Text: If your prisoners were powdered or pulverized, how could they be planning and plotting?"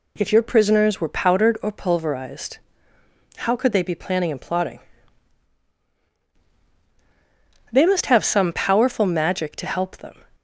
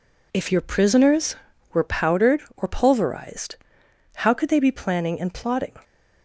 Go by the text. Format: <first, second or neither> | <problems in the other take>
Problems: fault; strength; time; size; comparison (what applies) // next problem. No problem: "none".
second | goes on to say "They must have some powerful magic to help them"; strong; from 7.7 s on; 2.5 s long